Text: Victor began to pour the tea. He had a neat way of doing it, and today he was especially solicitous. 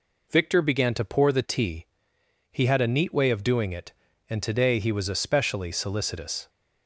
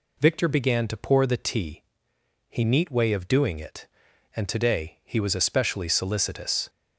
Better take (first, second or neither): first